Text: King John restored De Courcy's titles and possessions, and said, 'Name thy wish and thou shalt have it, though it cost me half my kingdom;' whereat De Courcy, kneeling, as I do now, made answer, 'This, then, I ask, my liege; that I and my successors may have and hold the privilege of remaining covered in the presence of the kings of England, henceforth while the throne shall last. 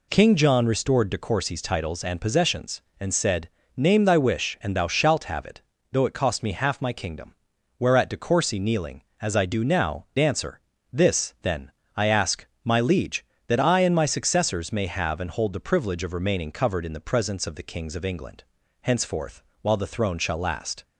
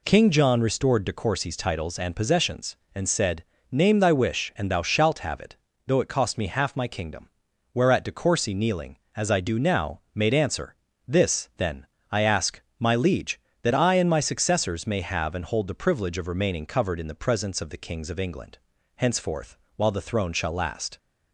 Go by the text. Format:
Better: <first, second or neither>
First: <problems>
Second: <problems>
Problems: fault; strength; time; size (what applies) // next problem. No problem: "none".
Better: second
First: skips "made"; at 10.1 s // pauses between "henceforth" and "while"; slight; at 19.4 s; 0.22 s long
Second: pauses between "henceforth" and "while"; slight; at 19.5 s; 0.22 s long